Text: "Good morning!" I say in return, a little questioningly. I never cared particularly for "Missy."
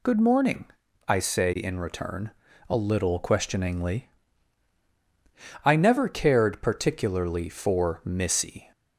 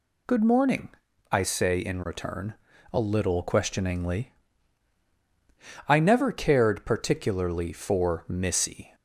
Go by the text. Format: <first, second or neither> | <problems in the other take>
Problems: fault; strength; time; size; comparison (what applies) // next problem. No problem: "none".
neither | none